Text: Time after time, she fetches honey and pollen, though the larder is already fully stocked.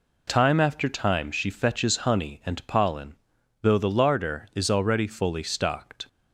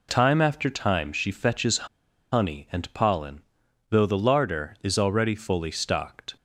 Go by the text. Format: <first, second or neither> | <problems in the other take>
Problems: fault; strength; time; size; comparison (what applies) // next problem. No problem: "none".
first | pauses between "fetches" and "honey"; noticeable; at 1.8 s; 0.46 s long